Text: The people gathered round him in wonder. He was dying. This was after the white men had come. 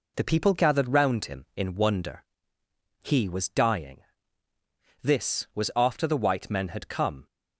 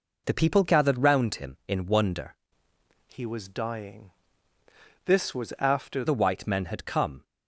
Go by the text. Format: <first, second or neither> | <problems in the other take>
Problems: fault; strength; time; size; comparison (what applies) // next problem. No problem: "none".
first | changes voice from "He" to "after"; from 3.1 to 6.0 s; 2.9 s long